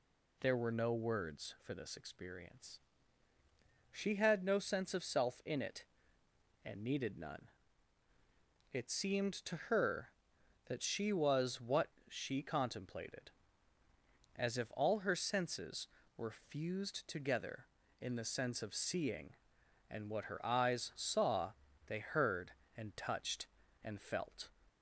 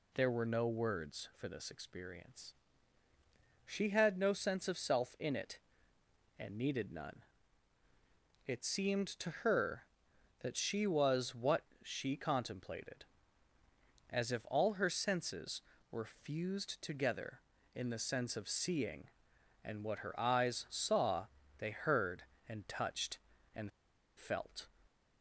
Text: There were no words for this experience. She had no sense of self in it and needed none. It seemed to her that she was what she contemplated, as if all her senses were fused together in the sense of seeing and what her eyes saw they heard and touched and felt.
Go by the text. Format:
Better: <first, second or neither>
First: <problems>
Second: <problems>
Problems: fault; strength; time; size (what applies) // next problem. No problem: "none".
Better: first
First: pauses between "what" and "she"; slight; at 11.8 s; 0.20 s long // pauses between "saw" and "they"; slight; at 21.5 s; 0.34 s long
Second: pauses between "what" and "she"; slight; at 11.6 s; 0.20 s long // pauses between "saw" and "they"; slight; at 21.2 s; 0.32 s long // pauses between "and" and "felt"; noticeable; at 23.7 s; 0.48 s long